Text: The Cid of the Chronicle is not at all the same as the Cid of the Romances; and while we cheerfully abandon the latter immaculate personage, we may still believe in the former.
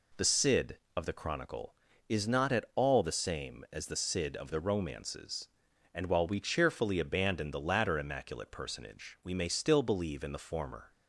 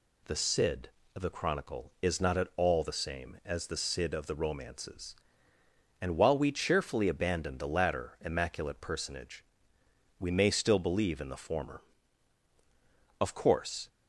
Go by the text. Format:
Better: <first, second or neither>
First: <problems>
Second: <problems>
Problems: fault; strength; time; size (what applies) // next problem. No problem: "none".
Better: first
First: none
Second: goes on to say "Of course"; noticeable; from 13.1 s on; 0.70 s long